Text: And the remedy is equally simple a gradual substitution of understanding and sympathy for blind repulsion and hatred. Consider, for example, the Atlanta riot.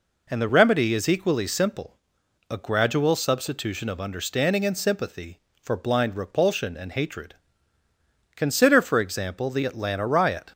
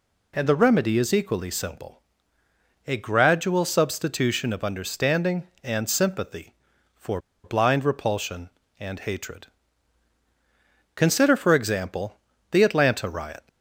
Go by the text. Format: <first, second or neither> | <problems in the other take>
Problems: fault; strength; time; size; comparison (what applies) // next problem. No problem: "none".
first | pauses between "simple" and "a"; noticeable; at 2.0 s; 0.86 s long; noticeable in the first // pauses between "for" and "blind"; slight; at 7.1 s; 0.25 s long